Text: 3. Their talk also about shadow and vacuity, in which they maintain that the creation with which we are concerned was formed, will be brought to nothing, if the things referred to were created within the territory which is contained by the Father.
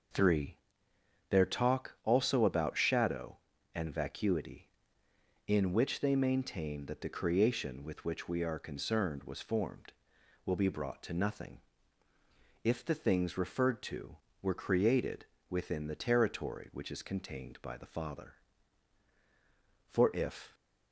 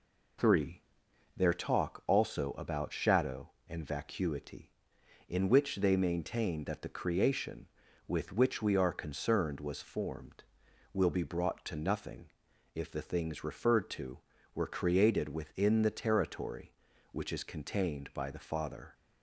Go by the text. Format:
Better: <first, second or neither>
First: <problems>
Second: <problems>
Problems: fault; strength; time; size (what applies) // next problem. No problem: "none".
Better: second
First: pauses between "created" and "within"; slight; at 15.2 s; 0.24 s long // goes on to say "For if"; noticeable; from 19.8 s on; 0.66 s long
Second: none